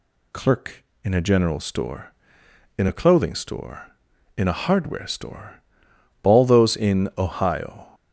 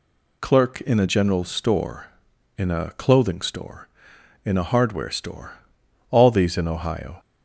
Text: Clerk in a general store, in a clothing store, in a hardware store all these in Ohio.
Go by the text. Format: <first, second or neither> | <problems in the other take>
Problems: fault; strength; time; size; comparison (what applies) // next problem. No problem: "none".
second | pauses between "store" and "all"; noticeable; at 5.5 s; 0.66 s long; noticeable in the second // says "those" for "these"; at 6.4 s